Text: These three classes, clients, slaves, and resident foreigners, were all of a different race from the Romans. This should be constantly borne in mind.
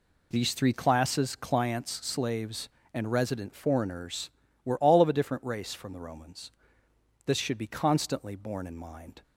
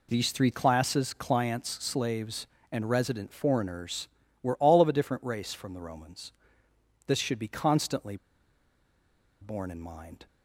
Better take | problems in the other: first | pauses between "constantly" and "borne"; strong; at 8.1 s; 1.2 s long

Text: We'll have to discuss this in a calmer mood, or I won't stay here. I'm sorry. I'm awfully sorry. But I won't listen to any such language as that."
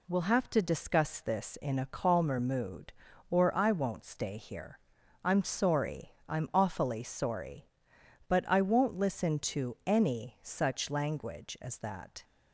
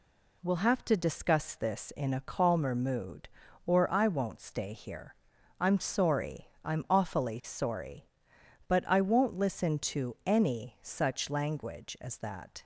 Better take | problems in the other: neither | none

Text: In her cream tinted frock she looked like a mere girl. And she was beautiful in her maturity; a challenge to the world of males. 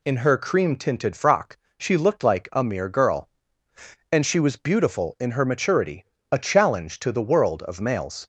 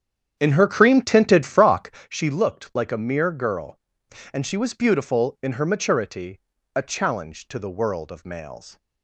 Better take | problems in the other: first | starts louder than the rest; strong; until 2.0 s; 9 dB // pauses between "frock" and "she"; slight; at 1.8 s; 0.20 s long; slight in the first

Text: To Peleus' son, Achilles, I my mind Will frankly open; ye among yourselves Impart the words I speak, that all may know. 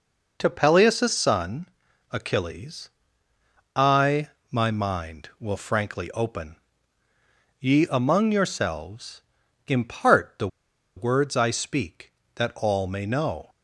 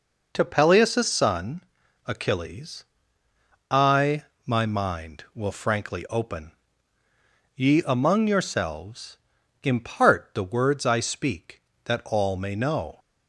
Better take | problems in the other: second | pauses between "I" and "my"; slight; at 4.2 s; 0.22 s long; slight in the second // pauses between "yourselves" and "Impart"; noticeable; at 9.2 s; 0.46 s long; noticeable in the second // pauses between "the" and "words"; noticeable; at 10.4 s; 0.49 s long

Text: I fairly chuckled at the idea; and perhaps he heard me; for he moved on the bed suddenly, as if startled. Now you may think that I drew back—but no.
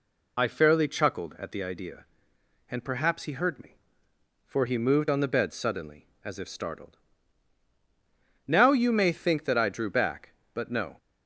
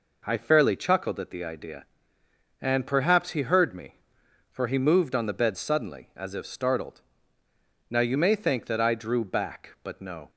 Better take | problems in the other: second | loses the start of "I"; at 0.3 s; 40 ms

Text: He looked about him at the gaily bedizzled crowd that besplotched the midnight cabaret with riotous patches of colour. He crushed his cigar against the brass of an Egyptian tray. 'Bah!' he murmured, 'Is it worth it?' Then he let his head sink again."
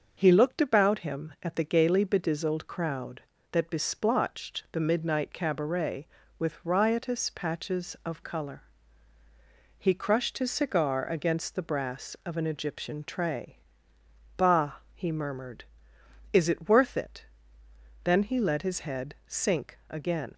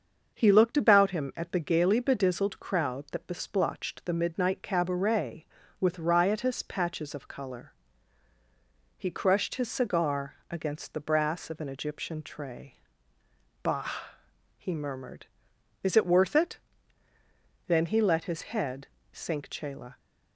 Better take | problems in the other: first | starts louder than the rest; until 1.3 s; 6.5 dB; also in the first // pauses between "head" and "sink"; slight; at 18.8 s; 0.24 s long // says "chela" for "again"; at 19.4 s

